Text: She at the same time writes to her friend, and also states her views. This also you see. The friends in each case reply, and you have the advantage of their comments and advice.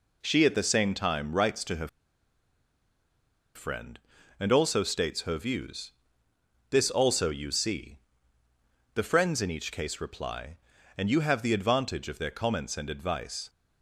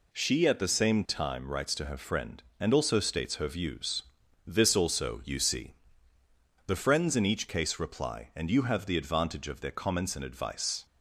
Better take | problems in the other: second | pauses between "her" and "friend"; strong; at 1.8 s; 1.6 s long

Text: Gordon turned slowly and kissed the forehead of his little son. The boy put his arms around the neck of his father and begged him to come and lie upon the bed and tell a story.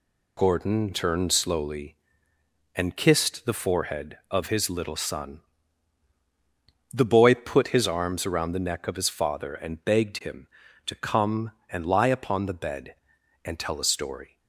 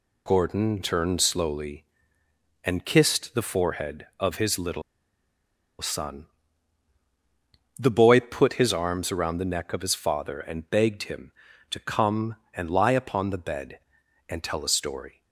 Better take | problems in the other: first | pauses between "little" and "son"; at 4.8 s; 0.99 s long

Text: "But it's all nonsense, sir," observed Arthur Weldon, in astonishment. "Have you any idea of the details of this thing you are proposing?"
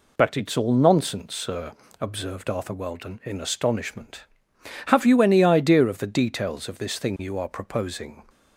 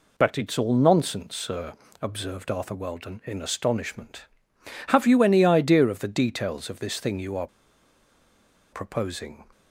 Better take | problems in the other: first | pauses between "are" and "proposing"; strong; at 7.4 s; 1.2 s long

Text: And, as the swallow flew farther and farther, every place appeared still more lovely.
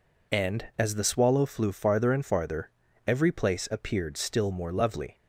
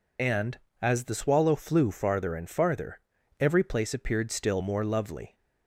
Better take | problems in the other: first | loses the start of "And"; at 0.1 s; 75 ms

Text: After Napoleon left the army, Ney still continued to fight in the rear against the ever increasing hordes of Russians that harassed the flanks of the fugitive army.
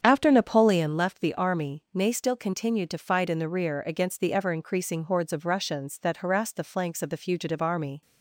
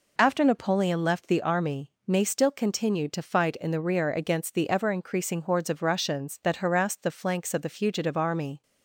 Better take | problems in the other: second | starts louder than the rest; strong; until 1.0 s; 8 dB

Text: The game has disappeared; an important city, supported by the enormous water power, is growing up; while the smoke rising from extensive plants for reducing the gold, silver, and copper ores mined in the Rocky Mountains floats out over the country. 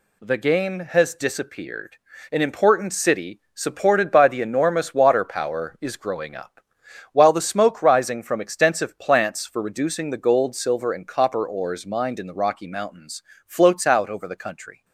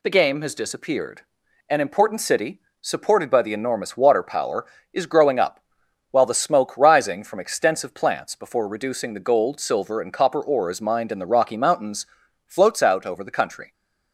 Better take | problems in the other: first | says "before" for "for"; at 8.3 s // pauses between "Mountains" and "floats"; at 12.0 s; 0.40 s long; slight in the first

